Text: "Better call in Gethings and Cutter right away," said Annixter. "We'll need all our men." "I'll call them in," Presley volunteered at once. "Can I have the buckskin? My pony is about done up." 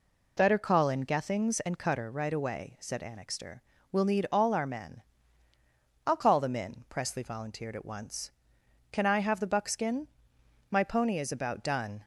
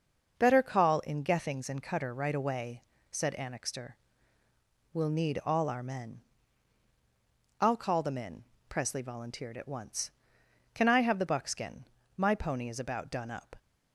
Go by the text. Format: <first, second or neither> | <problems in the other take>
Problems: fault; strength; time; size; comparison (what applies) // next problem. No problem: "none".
second | stops before "up"; at 12.0 s